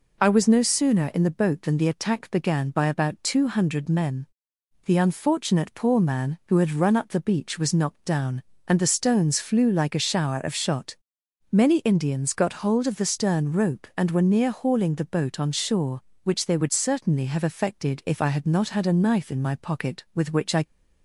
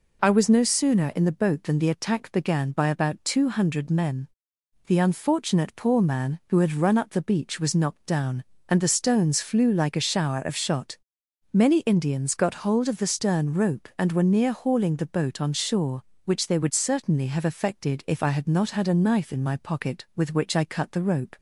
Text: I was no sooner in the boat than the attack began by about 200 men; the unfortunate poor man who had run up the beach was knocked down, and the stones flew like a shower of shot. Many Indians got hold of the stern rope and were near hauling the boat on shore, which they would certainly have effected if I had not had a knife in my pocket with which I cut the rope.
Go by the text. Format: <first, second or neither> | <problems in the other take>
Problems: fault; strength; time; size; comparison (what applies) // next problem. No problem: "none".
second | stops before "cut the rope"; at 20.6 s